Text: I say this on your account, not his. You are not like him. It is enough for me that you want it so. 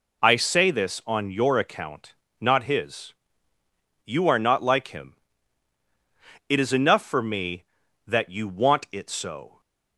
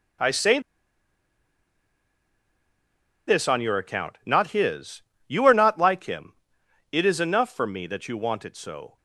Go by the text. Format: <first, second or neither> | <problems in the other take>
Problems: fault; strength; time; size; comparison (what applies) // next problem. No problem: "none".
first | pauses between "say" and "this"; strong; at 0.5 s; 2.6 s long